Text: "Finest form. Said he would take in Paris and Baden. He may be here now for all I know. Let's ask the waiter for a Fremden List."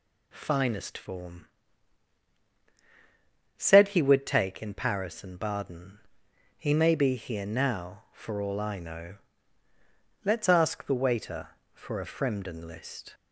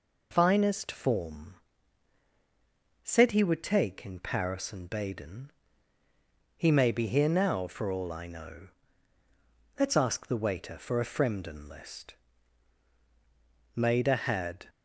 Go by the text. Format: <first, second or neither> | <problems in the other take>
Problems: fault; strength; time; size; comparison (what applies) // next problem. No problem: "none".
first | goes on to say "Maida had"; noticeable; from 13.7 s on; 0.92 s long